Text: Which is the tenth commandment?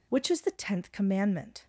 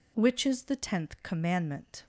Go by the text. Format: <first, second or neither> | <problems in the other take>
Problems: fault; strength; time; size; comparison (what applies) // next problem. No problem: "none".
neither | none